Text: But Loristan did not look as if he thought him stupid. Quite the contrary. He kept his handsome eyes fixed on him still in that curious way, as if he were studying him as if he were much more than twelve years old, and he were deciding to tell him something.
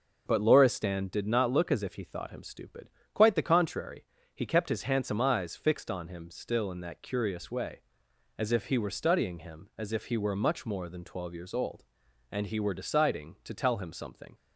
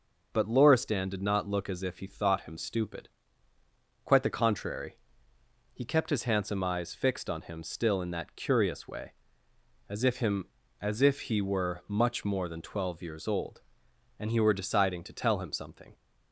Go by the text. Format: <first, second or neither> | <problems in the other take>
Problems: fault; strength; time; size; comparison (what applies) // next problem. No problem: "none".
first | skips "he were studying"; at 10.1 s